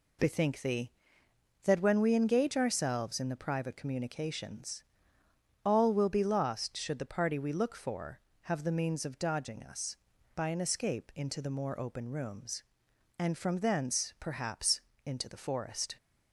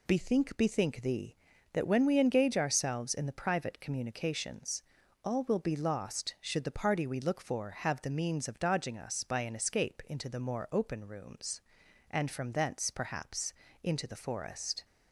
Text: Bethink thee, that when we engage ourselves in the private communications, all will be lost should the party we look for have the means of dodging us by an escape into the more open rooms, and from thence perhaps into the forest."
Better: first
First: pauses between "perhaps" and "into"; slight; at 14.7 s; 0.26 s long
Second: says "Bethink" twice; at 0.5 s // pauses between "perhaps" and "into"; slight; at 13.5 s; 0.30 s long

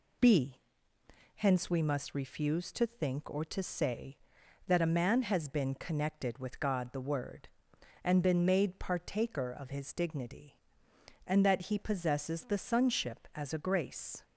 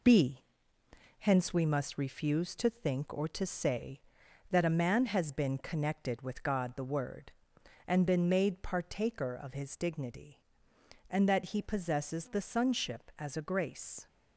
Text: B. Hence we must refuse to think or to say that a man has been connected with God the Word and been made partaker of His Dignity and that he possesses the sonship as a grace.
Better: first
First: none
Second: gets quieter; noticeable; throughout; 6 dB

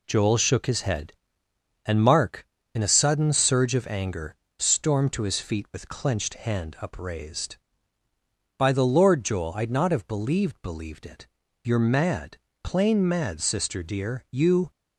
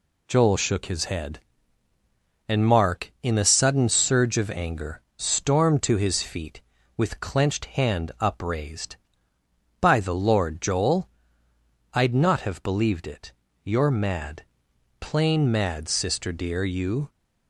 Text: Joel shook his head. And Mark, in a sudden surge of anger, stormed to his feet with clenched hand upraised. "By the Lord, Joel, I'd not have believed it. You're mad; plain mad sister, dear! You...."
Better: second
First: says "believed" twice; at 10.6 s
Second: none

